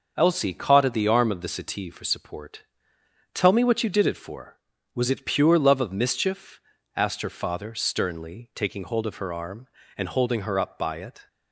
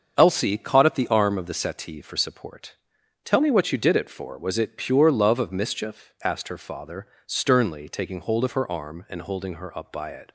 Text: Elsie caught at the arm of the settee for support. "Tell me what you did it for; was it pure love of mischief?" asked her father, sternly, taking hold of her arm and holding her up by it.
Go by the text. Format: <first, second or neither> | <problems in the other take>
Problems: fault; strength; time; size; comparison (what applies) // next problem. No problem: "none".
neither | starts louder than the rest; the same in both